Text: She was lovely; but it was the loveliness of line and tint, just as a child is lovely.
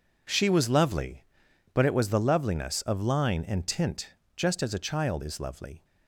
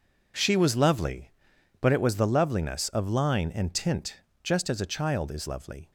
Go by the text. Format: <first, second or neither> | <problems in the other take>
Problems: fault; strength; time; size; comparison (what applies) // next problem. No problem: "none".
neither | none